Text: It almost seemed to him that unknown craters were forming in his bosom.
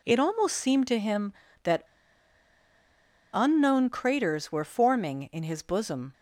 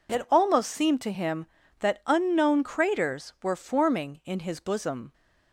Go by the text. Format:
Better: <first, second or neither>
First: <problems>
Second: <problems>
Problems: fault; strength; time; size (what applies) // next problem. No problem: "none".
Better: second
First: pauses between "that" and "unknown"; strong; at 1.8 s; 1.4 s long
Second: none